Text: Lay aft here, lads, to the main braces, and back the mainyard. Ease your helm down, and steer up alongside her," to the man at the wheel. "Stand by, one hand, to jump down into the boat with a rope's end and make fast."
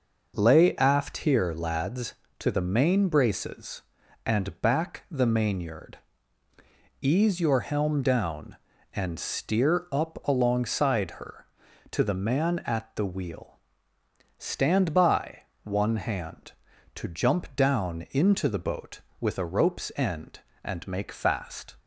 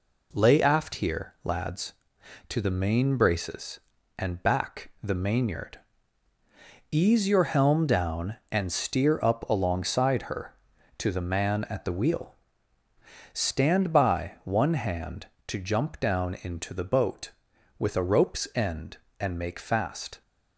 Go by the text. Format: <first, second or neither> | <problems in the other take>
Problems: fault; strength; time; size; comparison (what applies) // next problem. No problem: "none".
neither | none